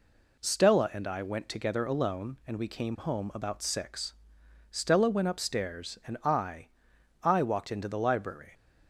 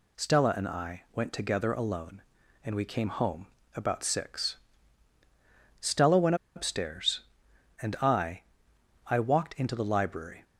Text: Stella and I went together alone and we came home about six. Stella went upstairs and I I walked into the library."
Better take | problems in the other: first | pauses between "home" and "about"; slight; at 3.4 s; 0.28 s long // pauses between "went" and "upstairs"; slight; at 6.3 s; 0.20 s long // pauses between "I" and "I"; noticeable; at 8.4 s; 0.64 s long; noticeable in the first

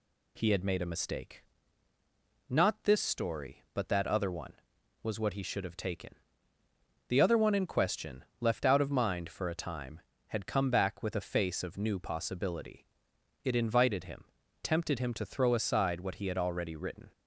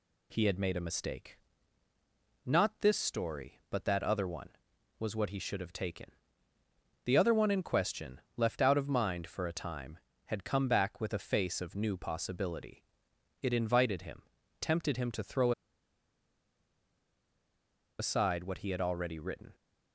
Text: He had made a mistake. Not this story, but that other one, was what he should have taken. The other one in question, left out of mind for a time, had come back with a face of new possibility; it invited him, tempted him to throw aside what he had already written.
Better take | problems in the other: first | pauses between "throw" and "aside"; strong; at 15.5 s; 2.4 s long

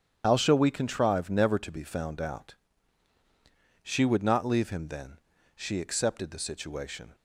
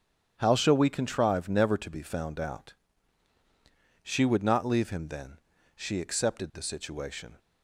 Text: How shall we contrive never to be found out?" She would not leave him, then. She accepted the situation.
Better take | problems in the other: second | loses the start of "How"; at 0.2 s; 40 ms // starts louder than the rest; strong; until 1.2 s; 9 dB; strong in the second

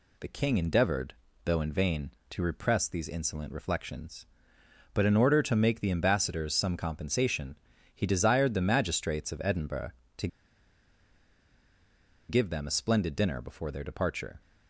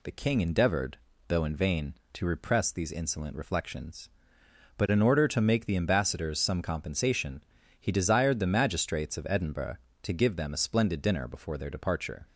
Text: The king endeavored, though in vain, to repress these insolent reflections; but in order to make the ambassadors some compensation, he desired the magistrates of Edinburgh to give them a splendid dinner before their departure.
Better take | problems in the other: second | pauses between "to" and "give"; strong; at 10.2 s; 2.0 s long

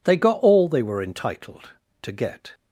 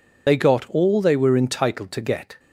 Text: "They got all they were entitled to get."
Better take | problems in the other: first | loses the start of "They"; at 0.2 s; 50 ms

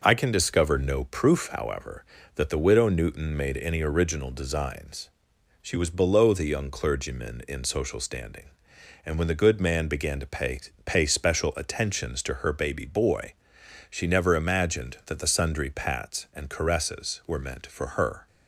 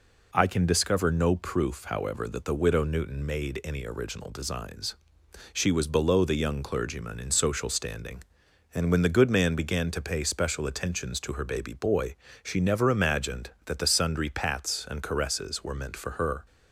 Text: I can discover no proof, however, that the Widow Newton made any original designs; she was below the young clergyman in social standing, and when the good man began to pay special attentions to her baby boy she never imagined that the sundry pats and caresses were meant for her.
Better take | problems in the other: second | says "pay" twice; at 10.8 s // pauses between "boy" and "she"; noticeable; at 13.3 s; 0.56 s long; slight in the second

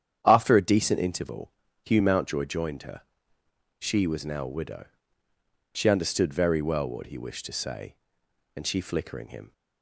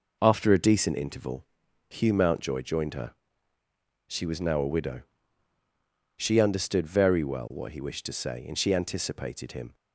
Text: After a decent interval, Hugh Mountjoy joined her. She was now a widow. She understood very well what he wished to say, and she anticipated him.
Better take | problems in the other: second | starts louder than the rest; strong; until 1.2 s; 9 dB // says "flickering" for "anticipated"; at 8.8 s

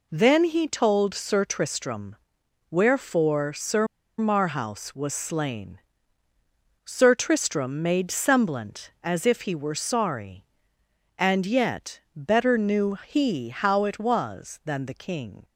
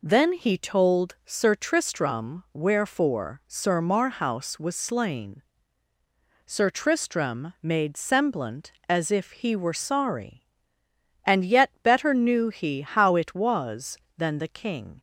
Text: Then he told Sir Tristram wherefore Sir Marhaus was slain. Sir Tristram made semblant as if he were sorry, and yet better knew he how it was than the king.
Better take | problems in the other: second | pauses between "Tristram" and "wherefore"; noticeable; at 2.1 s; 0.56 s long // pauses between "Sir" and "Marhaus"; slight; at 3.8 s; 0.33 s long

